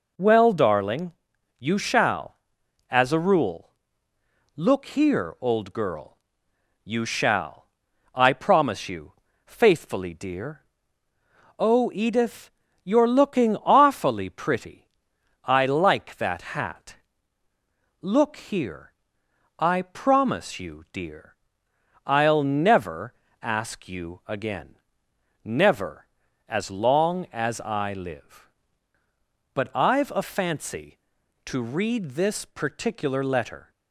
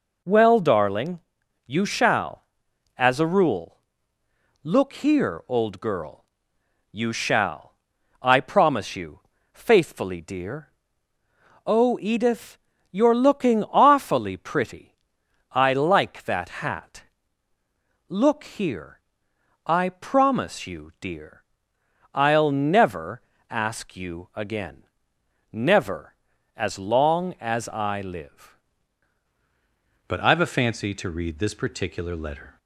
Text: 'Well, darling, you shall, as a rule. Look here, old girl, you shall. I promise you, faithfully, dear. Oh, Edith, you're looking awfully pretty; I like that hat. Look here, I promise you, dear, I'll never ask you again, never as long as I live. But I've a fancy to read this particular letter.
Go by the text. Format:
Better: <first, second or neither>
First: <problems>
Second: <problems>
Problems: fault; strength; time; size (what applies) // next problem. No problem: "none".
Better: first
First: pauses between "never" and "ask"; slight; at 23.1 s; 0.28 s long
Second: pauses between "never" and "ask"; slight; at 23.2 s; 0.28 s long // changes voice at "But"; from 30.0 s on; 2.5 s long